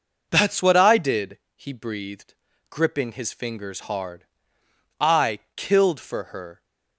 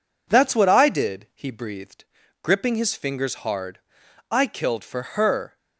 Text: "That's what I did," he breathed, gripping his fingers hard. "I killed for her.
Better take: neither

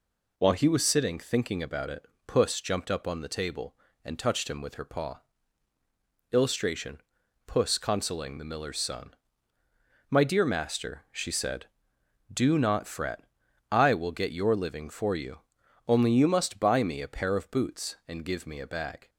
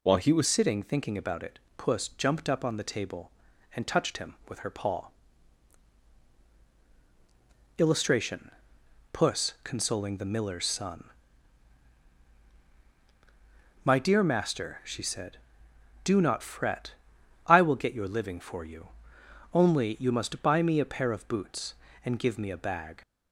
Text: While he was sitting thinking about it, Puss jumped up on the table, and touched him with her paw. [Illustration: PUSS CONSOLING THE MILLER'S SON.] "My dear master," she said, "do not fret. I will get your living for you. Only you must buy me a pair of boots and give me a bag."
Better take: first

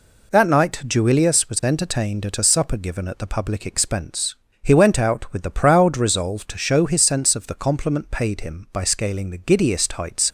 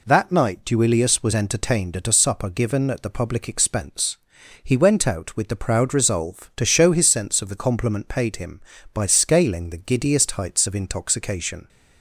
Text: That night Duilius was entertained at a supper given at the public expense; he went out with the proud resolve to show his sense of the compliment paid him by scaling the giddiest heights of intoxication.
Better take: second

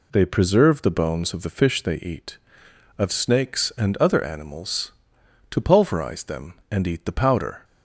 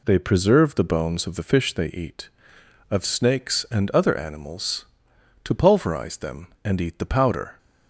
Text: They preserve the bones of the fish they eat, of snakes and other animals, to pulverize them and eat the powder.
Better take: neither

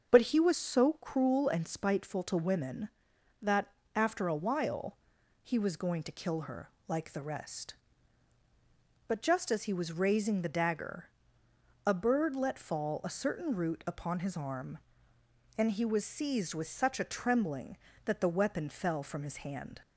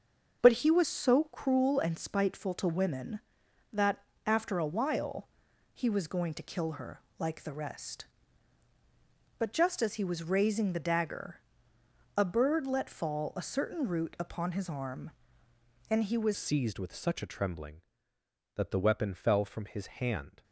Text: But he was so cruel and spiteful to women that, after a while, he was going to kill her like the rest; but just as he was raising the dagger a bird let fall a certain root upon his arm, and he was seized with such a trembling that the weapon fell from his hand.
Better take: first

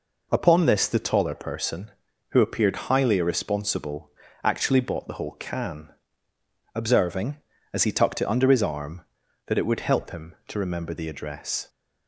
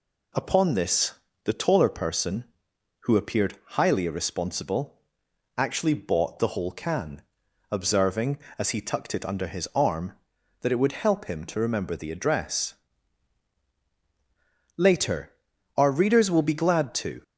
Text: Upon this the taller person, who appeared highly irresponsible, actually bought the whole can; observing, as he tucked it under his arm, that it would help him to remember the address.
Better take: first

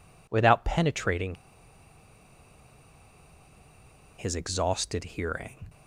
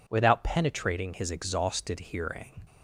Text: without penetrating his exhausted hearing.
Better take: second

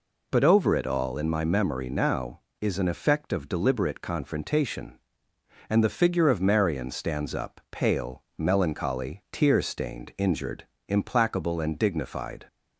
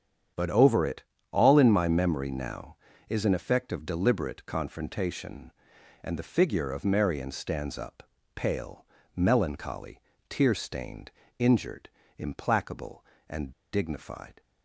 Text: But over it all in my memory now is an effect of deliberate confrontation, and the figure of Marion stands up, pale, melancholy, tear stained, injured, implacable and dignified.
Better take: first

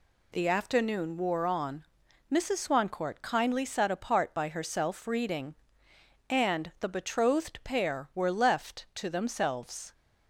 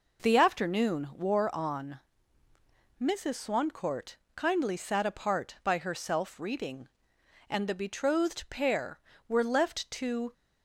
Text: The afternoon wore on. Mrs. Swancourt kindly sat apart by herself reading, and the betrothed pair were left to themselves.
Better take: first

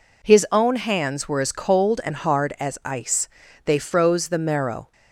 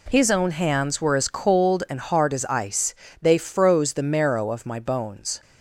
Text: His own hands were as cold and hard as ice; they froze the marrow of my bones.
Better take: second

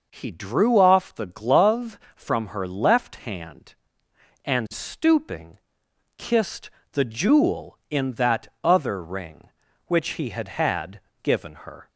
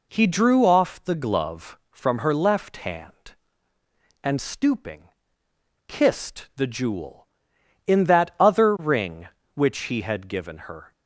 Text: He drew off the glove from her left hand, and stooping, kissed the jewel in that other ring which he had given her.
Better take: second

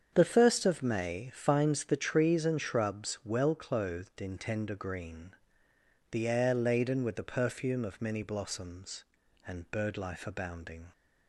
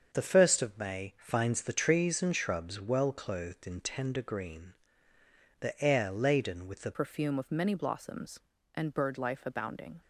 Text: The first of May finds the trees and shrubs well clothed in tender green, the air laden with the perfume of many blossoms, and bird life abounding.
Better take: first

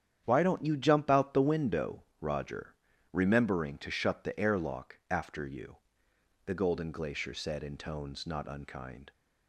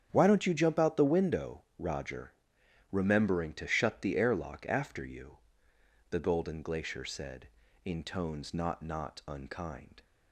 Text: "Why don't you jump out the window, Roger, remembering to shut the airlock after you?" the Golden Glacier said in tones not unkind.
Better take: first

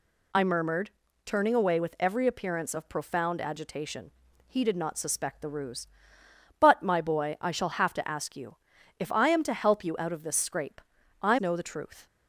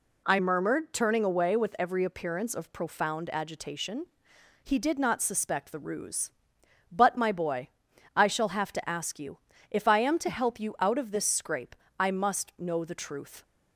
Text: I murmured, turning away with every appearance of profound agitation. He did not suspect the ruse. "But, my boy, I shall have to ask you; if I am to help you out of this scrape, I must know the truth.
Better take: second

